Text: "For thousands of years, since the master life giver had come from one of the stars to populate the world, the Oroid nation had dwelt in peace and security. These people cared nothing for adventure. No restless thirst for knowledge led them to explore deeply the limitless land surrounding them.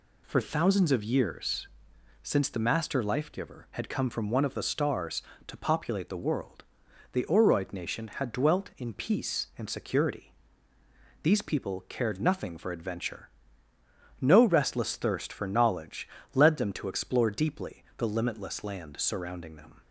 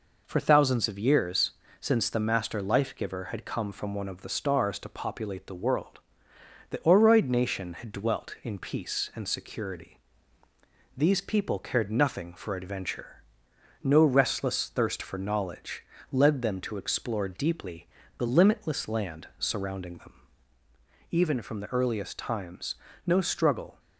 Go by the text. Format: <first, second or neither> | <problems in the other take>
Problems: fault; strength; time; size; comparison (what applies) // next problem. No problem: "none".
first | pauses between "knowledge" and "led"; slight; at 15.8 s; 0.28 s long; slight in the first // pauses between "deeply" and "the"; slight; at 17.8 s; 0.30 s long // goes on to say "Even from the earliest times no struggle"; strong; from 21.0 s on; 2.7 s long